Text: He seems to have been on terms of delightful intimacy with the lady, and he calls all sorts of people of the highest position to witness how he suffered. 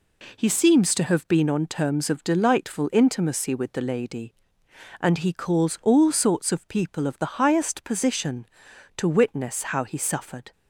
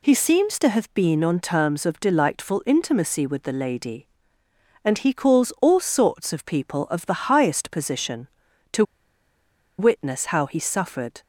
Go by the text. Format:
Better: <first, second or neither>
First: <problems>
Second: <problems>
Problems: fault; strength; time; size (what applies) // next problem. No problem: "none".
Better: first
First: none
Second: pauses between "to" and "witness"; noticeable; at 8.8 s; 0.94 s long